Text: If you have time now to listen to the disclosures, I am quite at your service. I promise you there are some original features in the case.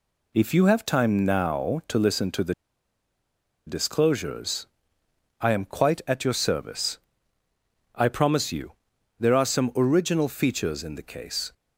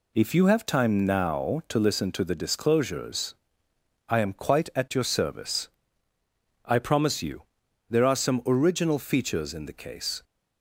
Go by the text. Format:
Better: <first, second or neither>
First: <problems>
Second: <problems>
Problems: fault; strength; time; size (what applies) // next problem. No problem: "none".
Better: second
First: pauses between "the" and "disclosures"; at 2.5 s; 1.1 s long // pauses between "you" and "there"; noticeable; at 8.7 s; 0.46 s long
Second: pauses between "you" and "there"; noticeable; at 7.4 s; 0.46 s long